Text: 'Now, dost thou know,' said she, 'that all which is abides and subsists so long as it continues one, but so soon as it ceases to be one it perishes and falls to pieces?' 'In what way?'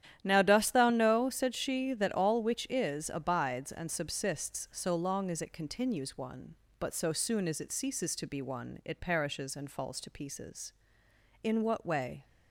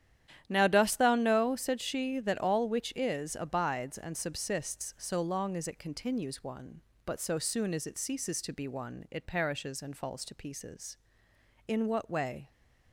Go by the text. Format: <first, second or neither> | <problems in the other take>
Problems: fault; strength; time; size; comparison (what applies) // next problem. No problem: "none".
neither | starts louder than the rest; strong; the same in both